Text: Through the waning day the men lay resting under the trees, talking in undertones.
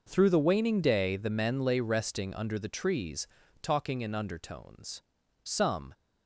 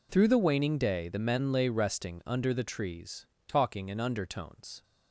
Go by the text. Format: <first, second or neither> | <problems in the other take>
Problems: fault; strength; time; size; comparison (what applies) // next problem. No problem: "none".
second | goes on to say "Some"; from 5.4 s on; 0.50 s long